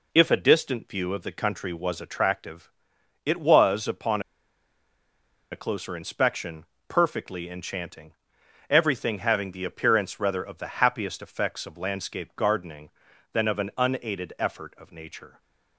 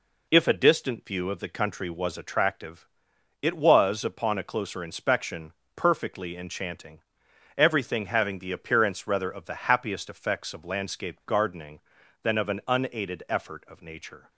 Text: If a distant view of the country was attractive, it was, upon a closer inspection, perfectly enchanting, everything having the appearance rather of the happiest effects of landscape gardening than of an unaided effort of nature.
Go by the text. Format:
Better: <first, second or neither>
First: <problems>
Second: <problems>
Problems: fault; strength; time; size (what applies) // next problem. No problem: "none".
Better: second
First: pauses between "upon" and "a"; strong; at 4.2 s; 1.3 s long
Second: none